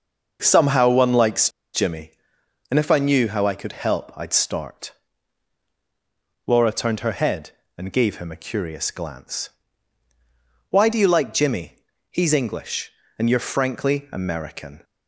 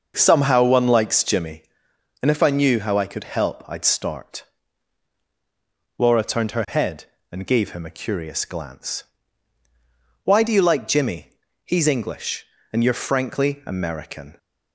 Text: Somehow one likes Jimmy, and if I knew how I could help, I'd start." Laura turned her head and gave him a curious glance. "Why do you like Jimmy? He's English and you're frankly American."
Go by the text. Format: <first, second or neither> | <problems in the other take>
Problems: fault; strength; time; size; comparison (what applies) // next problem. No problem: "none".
second | starts louder than the rest; noticeable; until 1.4 s; 6 dB; noticeable in the second // pauses between "likes" and "Jimmy"; slight; at 1.5 s; 0.22 s long